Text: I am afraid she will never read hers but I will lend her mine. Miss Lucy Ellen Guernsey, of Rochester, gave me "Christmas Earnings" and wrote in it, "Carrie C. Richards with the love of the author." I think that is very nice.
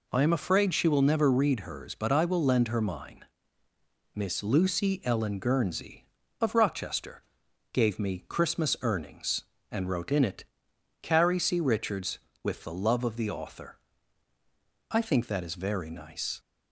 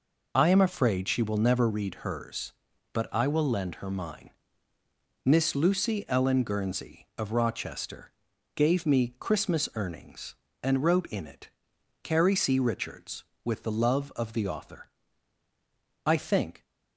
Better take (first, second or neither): first